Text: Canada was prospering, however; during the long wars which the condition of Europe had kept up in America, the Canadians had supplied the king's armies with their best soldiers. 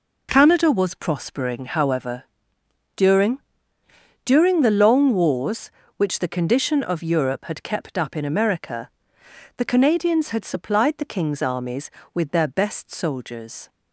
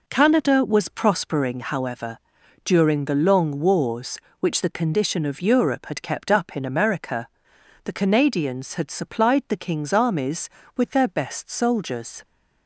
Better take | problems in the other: second | says "during" twice; at 4.2 s

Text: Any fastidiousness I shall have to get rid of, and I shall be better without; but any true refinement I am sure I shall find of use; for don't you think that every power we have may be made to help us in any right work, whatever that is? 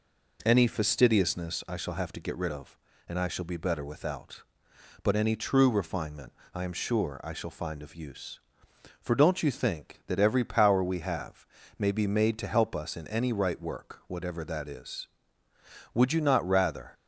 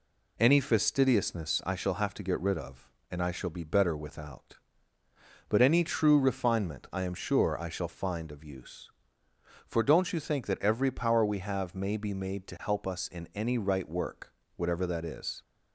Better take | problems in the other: second | pauses between "refinement" and "I"; slight; at 6.3 s; 0.22 s long // pauses between "have" and "may"; slight; at 11.4 s; 0.32 s long // goes on to say "Would you not rather"; noticeable; from 15.9 s on; 1.0 s long

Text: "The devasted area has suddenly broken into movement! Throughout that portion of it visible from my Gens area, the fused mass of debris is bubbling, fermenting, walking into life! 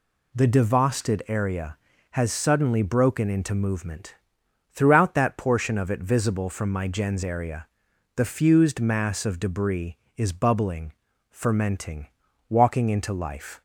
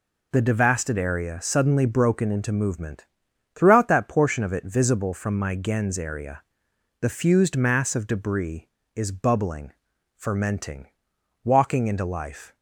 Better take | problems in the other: first | skips "has"; at 1.4 s

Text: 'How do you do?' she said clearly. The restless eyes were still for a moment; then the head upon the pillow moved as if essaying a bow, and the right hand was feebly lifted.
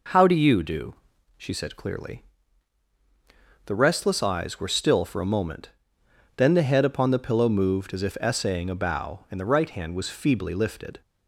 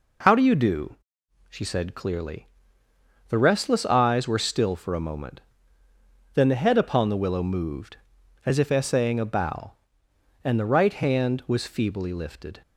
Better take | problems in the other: first | says "willow" for "pillow"; at 7.1 s

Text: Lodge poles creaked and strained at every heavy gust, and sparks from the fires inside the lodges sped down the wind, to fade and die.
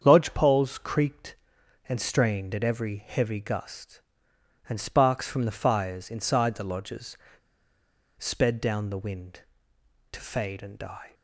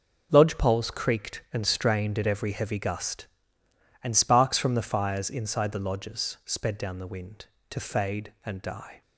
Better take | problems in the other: second | starts louder than the rest; strong; until 1.0 s; 7.5 dB // pauses between "lodges" and "sped"; at 7.1 s; 1.0 s long

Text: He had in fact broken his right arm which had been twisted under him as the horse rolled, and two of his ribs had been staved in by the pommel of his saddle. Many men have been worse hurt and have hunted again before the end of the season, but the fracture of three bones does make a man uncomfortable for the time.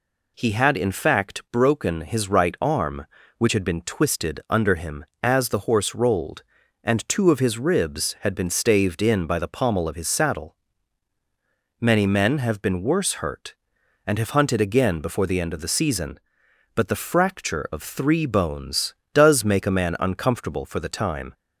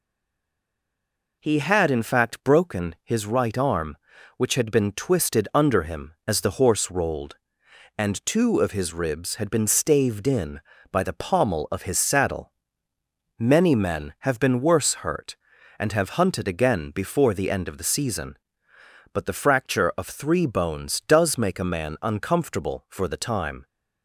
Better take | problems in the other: first | stays silent before the first word; noticeable; until 1.3 s; 1.3 s long

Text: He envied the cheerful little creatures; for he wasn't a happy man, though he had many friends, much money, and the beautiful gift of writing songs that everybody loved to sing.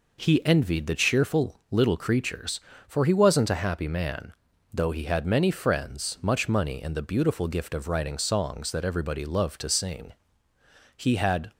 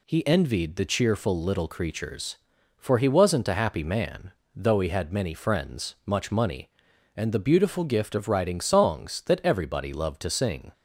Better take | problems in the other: second | goes on to say "He had"; from 10.9 s on; 0.54 s long

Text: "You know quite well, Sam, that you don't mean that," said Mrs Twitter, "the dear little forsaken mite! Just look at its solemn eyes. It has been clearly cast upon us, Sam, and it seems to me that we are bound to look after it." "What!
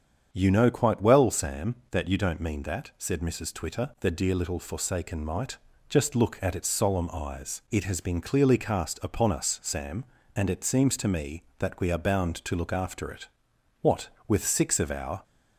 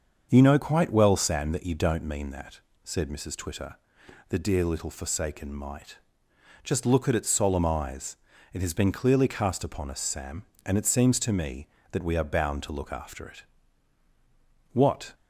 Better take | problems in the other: second | starts louder than the rest; strong; until 1.3 s; 8 dB; also in the second // goes on to say "with six of our"; noticeable; from 14.2 s on; 0.96 s long

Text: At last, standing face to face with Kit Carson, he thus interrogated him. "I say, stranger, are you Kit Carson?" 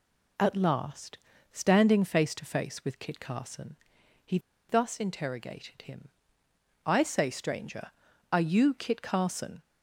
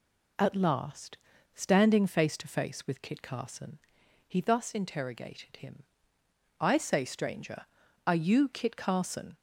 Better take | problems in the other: second | pauses between "he" and "thus"; slight; at 4.3 s; 0.30 s long

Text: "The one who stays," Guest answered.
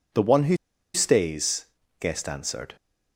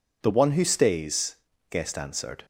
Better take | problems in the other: second | pauses between "who" and "stays"; at 0.5 s; 0.38 s long

